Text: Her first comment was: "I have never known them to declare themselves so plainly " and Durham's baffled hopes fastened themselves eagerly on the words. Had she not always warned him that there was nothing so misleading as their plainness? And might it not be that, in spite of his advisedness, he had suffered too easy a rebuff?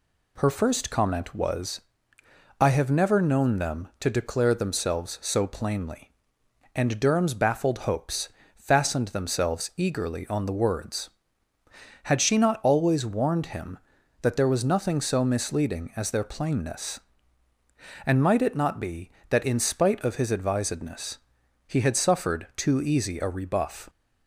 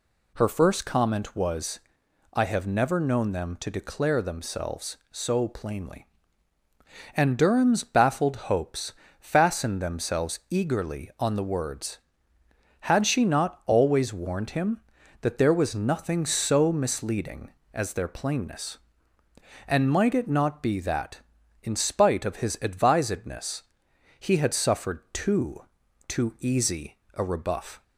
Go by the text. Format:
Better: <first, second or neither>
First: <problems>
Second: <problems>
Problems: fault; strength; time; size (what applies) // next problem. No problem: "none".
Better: first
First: pauses between "hopes" and "fastened"; slight; at 8.2 s; 0.26 s long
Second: pauses between "hopes" and "fastened"; slight; at 8.9 s; 0.26 s long // says "too" twice; at 26.0 s // pauses between "easy" and "a"; slight; at 26.9 s; 0.16 s long